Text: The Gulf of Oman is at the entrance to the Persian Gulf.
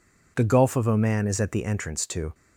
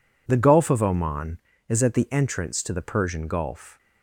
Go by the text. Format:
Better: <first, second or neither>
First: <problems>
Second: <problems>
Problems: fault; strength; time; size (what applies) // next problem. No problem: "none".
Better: second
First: stops before "the Persian Gulf"; at 2.3 s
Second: none